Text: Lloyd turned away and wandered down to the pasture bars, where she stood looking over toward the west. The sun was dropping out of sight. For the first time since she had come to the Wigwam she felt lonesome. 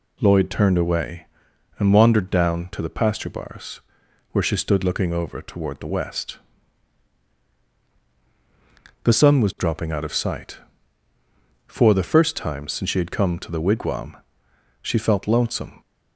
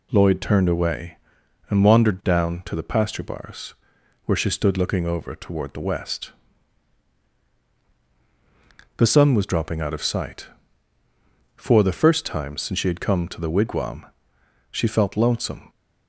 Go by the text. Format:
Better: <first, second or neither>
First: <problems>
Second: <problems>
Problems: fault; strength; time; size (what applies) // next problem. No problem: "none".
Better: neither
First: pauses between "Wigwam" and "she"; noticeable; at 14.1 s; 0.66 s long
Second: pauses between "Wigwam" and "she"; noticeable; at 14.0 s; 0.66 s long